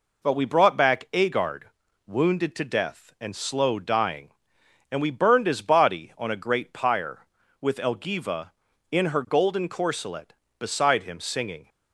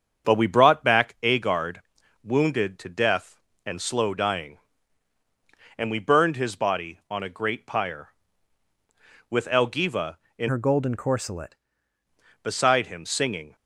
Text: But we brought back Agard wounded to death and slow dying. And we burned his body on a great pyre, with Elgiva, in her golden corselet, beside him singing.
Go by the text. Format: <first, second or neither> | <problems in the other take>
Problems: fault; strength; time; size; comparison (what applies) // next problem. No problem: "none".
first | starts louder than the rest; strong; until 1.3 s; 7.5 dB // pauses between "Agard" and "wounded"; noticeable; at 1.7 s; 0.46 s long; also in the first // changes voice from "her" to "corselet"; from 10.4 to 11.5 s; 1.1 s long